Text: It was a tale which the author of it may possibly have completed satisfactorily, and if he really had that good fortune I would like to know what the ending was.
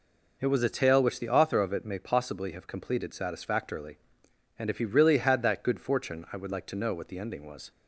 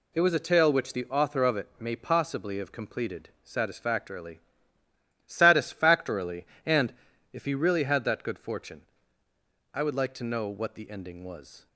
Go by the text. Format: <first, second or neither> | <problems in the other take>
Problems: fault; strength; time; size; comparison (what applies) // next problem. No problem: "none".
first | says "satisfactorily" twice; at 5.2 s // pauses between "and" and "if"; at 6.9 s; 0.40 s long // pauses between "fortune" and "I"; noticeable; at 8.8 s; 0.90 s long